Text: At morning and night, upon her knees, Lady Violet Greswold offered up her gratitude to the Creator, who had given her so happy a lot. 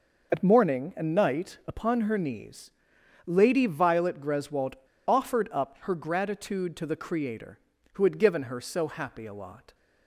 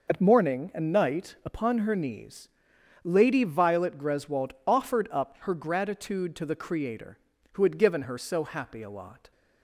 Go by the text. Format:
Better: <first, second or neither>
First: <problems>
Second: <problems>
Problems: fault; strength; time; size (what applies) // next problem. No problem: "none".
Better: second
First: pauses between "Greswold" and "offered"; slight; at 4.7 s; 0.32 s long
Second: none